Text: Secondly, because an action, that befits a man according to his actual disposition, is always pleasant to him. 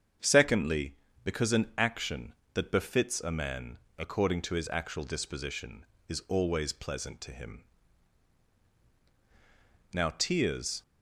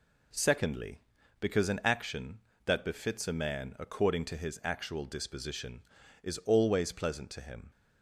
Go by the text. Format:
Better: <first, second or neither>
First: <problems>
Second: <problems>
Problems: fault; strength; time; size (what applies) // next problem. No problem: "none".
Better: second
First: starts louder than the rest; strong; until 1.5 s; 7.5 dB // pauses between "man" and "according"; slight; at 3.7 s; 0.20 s long // goes on to say "Now tears"; noticeable; from 9.9 s on; 0.90 s long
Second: none